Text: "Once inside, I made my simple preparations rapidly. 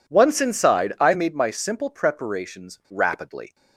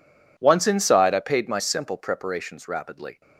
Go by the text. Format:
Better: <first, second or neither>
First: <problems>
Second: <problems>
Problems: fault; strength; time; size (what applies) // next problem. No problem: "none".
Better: first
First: none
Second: says "paid" for "made"; at 1.2 s